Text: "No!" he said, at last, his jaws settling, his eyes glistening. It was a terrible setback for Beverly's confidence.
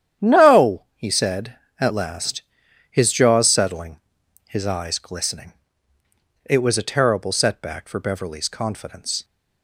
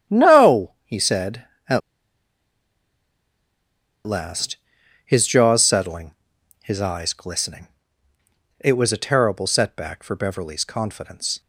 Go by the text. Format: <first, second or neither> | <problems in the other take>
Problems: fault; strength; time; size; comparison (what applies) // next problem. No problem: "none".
first | starts louder than the rest; strong; until 1.2 s; 9.5 dB; strong in the first // pauses between "at" and "last"; strong; at 1.8 s; 2.2 s long